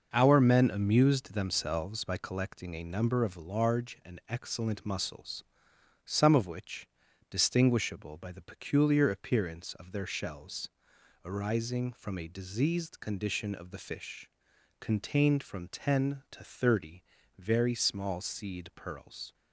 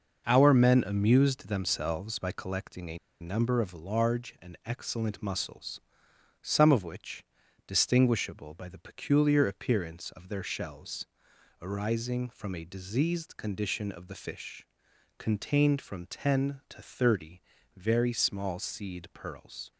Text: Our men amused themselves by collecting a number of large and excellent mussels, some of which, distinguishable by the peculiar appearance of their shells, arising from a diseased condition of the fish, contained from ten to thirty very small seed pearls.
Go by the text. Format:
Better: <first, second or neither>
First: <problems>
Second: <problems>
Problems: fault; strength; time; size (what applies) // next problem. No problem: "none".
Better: first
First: pauses between "thirty" and "very"; at 17.0 s; 0.38 s long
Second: pauses between "a" and "number"; slight; at 2.9 s; 0.23 s long // pauses between "thirty" and "very"; at 17.3 s; 0.38 s long